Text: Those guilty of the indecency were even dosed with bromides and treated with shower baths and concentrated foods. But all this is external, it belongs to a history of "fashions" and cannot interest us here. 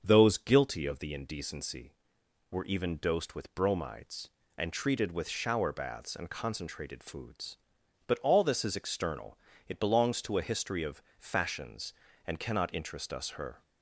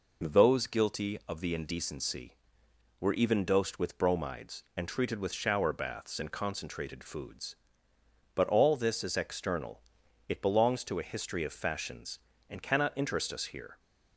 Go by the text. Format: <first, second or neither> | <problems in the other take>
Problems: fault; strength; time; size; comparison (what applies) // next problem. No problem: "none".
second | starts louder than the rest; until 1.0 s; 6.5 dB // pauses between "of" and "fashions"; slight; at 11.0 s; 0.16 s long // says "her" for "here"; at 13.3 s